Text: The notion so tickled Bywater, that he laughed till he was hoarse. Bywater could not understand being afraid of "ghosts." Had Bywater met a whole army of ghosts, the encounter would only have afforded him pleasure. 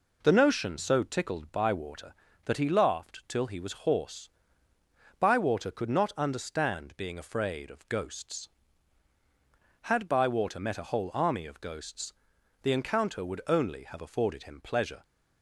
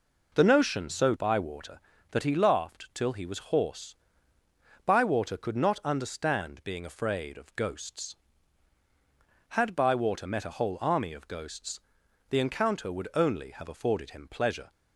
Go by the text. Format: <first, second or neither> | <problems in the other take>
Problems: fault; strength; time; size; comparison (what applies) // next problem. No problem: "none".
first | skips "tickled"; at 1.1 s